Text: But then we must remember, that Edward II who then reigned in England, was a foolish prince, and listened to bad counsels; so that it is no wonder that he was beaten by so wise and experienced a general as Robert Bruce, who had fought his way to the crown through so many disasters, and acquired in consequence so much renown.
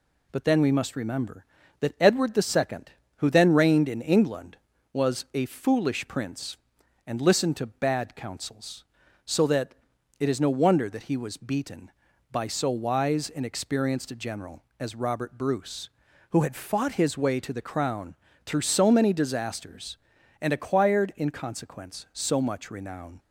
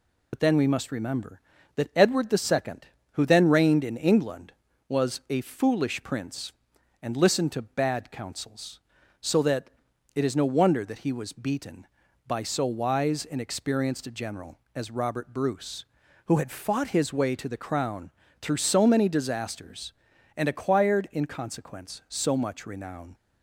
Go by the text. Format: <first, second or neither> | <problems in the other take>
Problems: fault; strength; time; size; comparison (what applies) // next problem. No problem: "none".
first | loses the start of "But"; at 0.3 s; 65 ms // pauses between "that" and "it"; noticeable; at 9.7 s; 0.46 s long; noticeable in the first // pauses between "crown" and "through"; slight; at 18.1 s; 0.30 s long; slight in the first